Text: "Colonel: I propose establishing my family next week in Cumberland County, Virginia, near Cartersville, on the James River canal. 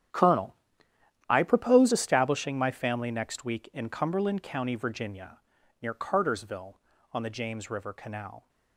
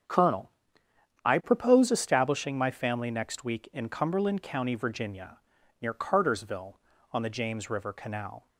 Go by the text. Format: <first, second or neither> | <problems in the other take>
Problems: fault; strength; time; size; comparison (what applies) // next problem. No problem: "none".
second | gets quieter; strong; throughout; 15 dB // starts louder than the rest; strong; until 1.8 s; 10 dB; strong in the second